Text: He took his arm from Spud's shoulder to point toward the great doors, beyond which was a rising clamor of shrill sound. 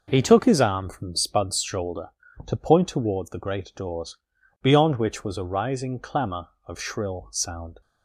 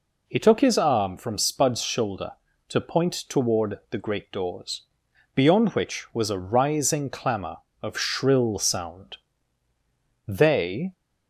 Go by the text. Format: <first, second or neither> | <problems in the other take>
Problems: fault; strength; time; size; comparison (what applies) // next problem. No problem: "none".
first | goes on to say "They"; noticeable; from 10.2 s on; 0.66 s long